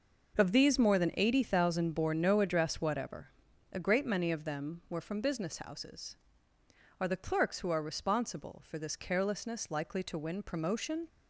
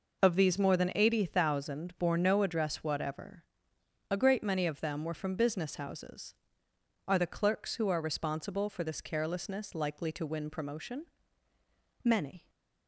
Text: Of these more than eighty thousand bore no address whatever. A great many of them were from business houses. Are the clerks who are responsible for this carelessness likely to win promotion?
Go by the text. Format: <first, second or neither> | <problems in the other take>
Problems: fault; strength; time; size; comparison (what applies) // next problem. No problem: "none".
first | goes on to say "Many"; slight; from 12.0 s on; 0.46 s long